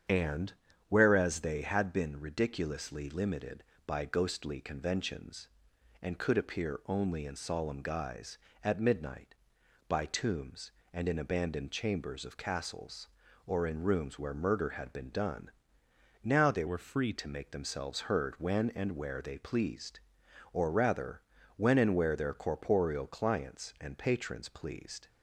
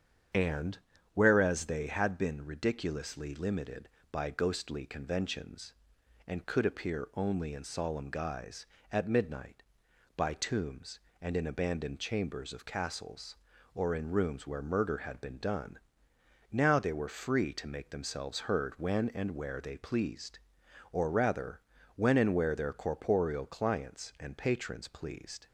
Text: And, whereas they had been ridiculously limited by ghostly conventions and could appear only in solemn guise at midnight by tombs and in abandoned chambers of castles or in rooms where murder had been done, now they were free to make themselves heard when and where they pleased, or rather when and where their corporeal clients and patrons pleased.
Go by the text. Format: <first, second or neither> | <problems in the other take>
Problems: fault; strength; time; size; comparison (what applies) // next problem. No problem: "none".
second | starts louder than the rest; strong; until 1.4 s; 8 dB; strong in the second // changes voice from "were" to "free"; from 16.6 to 17.1 s; 0.5 s long // pauses between "rather" and "when"; slight; at 21.2 s; 0.36 s long; slight in the second